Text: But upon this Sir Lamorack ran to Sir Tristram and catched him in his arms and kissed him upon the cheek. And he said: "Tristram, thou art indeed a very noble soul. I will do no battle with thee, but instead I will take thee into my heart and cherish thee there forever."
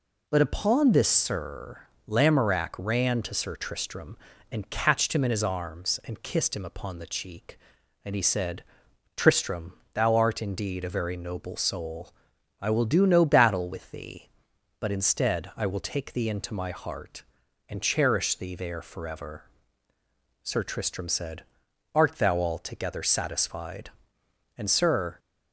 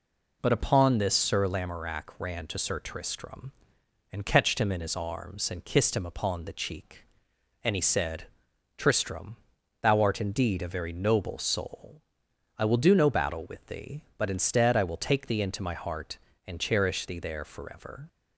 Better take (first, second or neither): second